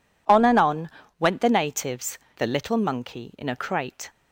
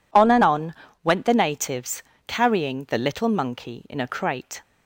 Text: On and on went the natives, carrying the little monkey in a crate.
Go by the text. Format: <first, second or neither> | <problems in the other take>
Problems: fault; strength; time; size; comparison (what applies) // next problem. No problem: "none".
second | pauses between "on" and "went"; slight; at 0.9 s; 0.28 s long; slight in the second // skips "carrying"; at 2.2 s